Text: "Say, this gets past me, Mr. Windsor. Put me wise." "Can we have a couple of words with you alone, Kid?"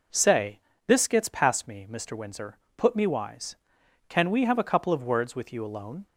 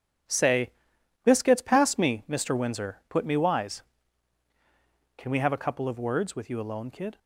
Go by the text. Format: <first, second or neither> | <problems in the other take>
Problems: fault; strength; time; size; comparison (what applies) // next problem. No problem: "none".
second | stops before "Kid"; at 6.0 s